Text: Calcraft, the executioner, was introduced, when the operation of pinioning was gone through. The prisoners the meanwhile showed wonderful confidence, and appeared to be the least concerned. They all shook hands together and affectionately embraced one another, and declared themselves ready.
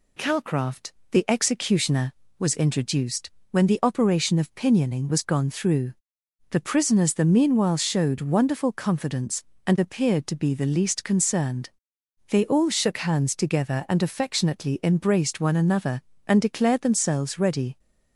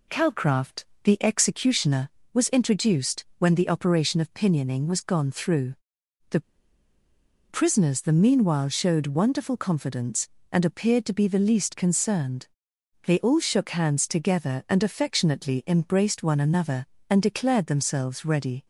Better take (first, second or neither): first